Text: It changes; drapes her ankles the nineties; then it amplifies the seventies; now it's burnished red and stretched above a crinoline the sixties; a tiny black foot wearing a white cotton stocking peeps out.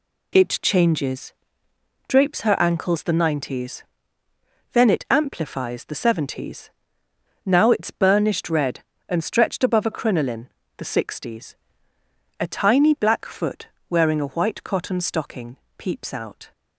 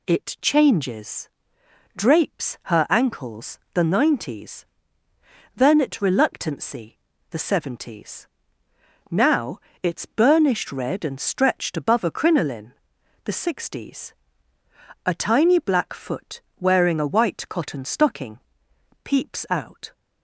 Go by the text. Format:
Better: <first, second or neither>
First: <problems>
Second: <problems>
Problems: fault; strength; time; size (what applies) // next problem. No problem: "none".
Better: first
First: pauses between "crinoline" and "the"; slight; at 10.4 s; 0.30 s long // pauses between "foot" and "wearing"; slight; at 13.6 s; 0.24 s long // pauses between "stocking" and "peeps"; slight; at 15.5 s; 0.20 s long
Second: pauses between "ankles" and "the"; slight; at 3.5 s; 0.16 s long // says "reluctancy" for "amplifies"; at 6.0 s // pauses between "now" and "it's"; slight; at 9.6 s; 0.20 s long // pauses between "crinoline" and "the"; noticeable; at 12.7 s; 0.50 s long // pauses between "foot" and "wearing"; slight; at 16.4 s; 0.18 s long // pauses between "stocking" and "peeps"; noticeable; at 18.3 s; 0.66 s long